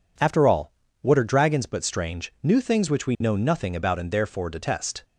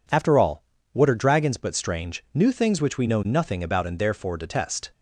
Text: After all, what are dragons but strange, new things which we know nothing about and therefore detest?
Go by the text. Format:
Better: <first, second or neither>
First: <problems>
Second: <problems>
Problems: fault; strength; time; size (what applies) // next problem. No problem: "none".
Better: neither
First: none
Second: none